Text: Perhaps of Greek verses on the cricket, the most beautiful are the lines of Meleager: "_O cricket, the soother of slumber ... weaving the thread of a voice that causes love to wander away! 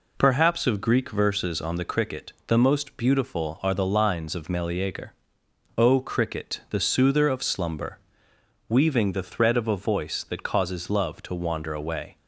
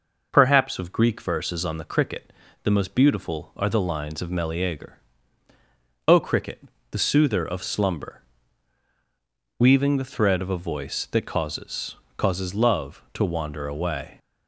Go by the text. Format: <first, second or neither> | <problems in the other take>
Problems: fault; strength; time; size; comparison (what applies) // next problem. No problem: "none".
first | says "causes" twice; at 12.1 s